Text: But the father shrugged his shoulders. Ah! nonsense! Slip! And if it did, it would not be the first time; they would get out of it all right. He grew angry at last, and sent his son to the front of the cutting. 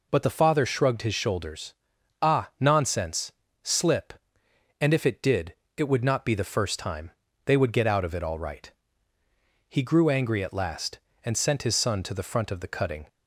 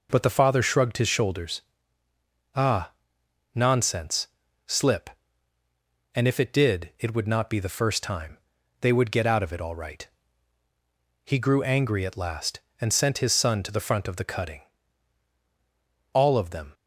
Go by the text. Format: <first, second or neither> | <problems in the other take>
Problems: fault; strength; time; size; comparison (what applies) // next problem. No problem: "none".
first | goes on to say "All of them"; noticeable; from 16.1 s on; 0.62 s long